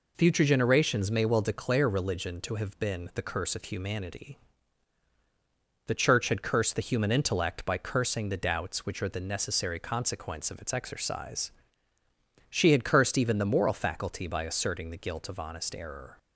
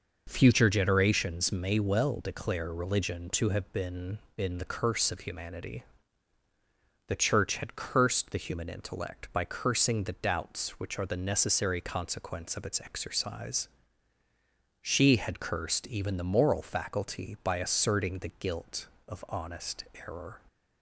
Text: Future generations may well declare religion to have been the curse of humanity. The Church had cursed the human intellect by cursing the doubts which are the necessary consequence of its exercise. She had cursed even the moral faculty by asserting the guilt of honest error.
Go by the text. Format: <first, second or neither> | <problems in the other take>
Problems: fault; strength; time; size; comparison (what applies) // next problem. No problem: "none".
first | says "been" twice; at 4.3 s // pauses between "honest" and "error"; slight; at 19.8 s; 0.20 s long